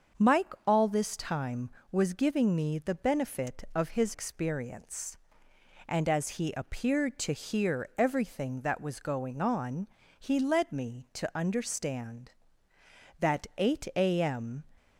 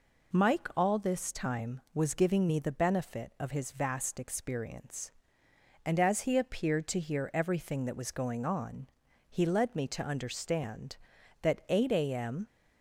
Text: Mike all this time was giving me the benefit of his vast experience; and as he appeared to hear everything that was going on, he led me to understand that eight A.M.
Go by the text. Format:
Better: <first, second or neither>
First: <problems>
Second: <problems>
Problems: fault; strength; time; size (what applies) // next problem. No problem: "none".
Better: second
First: starts louder than the rest; until 1.3 s; 7 dB // skips "vast"; at 4.1 s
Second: none